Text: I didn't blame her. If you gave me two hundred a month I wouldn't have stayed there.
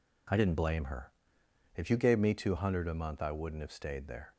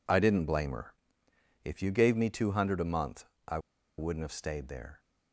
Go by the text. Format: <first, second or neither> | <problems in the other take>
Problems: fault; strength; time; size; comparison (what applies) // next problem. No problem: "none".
first | pauses between "month" and "I"; slight; at 3.2 s; 0.24 s long // pauses between "I" and "wouldn't"; at 3.5 s; 0.39 s long